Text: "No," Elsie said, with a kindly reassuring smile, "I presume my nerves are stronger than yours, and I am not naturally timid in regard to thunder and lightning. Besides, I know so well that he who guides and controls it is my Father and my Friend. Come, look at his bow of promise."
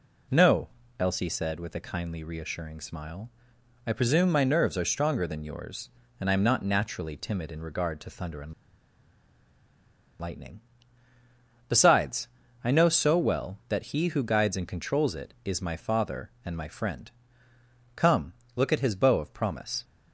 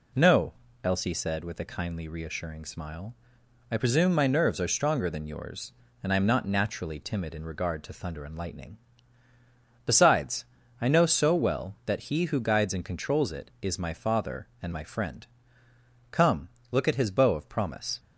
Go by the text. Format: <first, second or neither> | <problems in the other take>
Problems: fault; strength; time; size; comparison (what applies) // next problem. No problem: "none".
second | pauses between "and" and "lightning"; strong; at 8.5 s; 1.6 s long